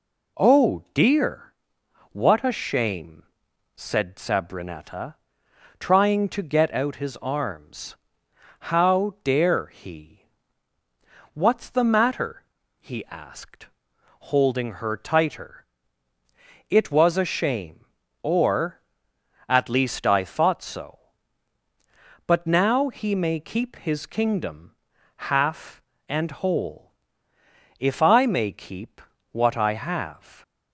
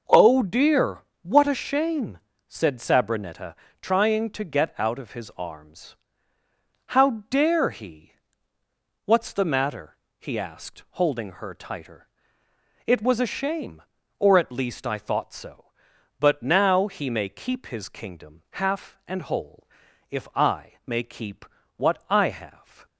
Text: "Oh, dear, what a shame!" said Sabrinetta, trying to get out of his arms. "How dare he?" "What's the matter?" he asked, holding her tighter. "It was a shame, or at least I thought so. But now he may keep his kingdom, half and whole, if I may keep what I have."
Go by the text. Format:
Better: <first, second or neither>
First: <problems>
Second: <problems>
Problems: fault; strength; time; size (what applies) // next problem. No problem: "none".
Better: second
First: skips "of"; at 6.9 s // pauses between "keep" and "what"; slight; at 29.0 s; 0.32 s long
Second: pauses between "keep" and "what"; slight; at 21.4 s; 0.34 s long